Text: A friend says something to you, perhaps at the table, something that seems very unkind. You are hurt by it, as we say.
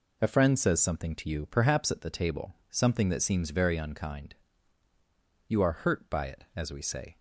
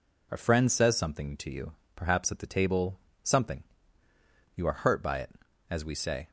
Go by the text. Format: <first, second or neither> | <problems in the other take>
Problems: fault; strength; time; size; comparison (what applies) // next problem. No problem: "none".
first | skips "that seems very unkind"; at 4.0 s